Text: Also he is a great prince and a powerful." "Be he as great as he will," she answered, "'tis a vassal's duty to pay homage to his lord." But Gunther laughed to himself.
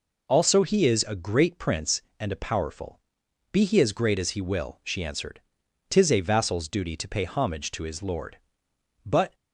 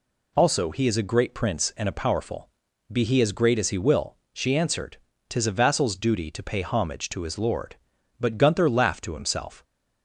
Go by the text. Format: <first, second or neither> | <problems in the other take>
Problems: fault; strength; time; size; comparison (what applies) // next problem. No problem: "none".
second | stops before "Gunther laughed to himself"; at 9.3 s